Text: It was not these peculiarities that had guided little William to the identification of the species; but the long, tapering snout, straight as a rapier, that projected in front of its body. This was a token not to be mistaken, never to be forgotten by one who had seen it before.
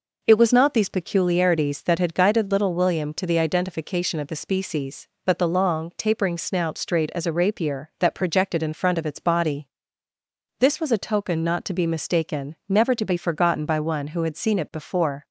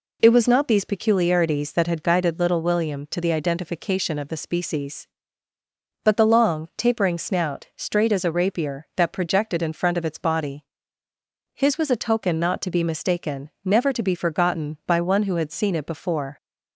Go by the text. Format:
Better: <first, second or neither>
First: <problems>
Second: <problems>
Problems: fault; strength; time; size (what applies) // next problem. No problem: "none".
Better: first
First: none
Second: says "His" for "This"; at 11.5 s